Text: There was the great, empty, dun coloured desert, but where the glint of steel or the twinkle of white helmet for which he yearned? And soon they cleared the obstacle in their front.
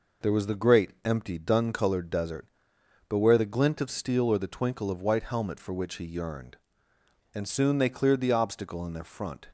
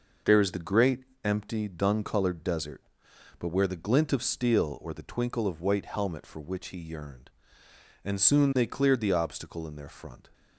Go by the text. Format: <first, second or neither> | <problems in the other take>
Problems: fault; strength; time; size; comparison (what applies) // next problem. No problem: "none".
first | says "is" for "was"; at 0.3 s